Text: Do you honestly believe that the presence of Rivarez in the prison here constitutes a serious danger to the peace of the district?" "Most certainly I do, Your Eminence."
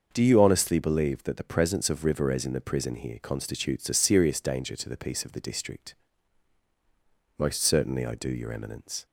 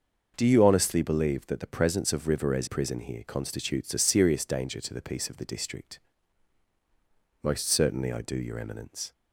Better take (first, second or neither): first